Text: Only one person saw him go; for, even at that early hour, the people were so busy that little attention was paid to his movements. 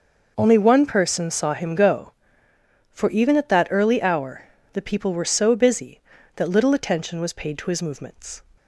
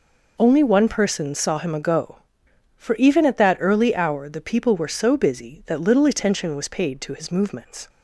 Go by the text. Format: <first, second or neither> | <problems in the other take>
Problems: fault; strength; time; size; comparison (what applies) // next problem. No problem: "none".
first | says "ago" for "go"; at 1.7 s